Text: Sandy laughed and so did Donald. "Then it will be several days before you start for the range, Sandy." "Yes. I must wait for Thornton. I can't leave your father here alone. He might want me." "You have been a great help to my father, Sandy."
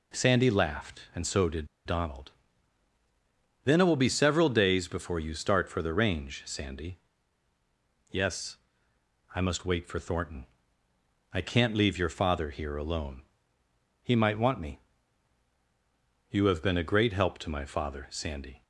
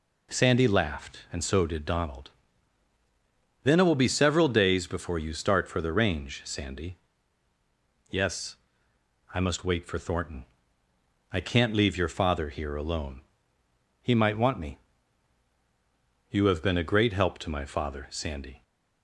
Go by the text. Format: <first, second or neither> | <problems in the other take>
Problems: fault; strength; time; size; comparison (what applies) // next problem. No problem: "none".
second | pauses between "did" and "Donald"; slight; at 1.6 s; 0.19 s long